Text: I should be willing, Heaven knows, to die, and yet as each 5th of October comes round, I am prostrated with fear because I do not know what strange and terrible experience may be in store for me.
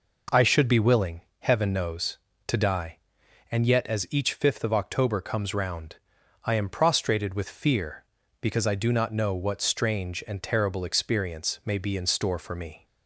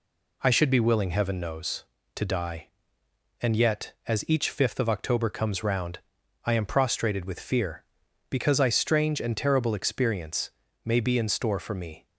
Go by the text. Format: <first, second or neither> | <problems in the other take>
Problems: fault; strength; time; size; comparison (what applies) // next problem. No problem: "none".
first | skips "do not know what"; at 8.6 s // pauses between "experience" and "may"; slight; at 10.5 s; 0.34 s long